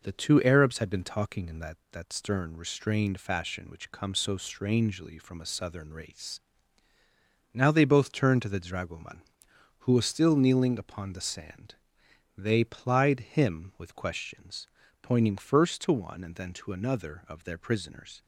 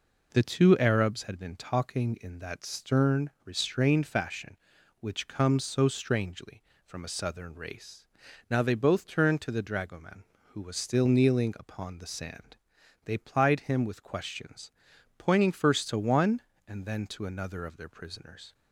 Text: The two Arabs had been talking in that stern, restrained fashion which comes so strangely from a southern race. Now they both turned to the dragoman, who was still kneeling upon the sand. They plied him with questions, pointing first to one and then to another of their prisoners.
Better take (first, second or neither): second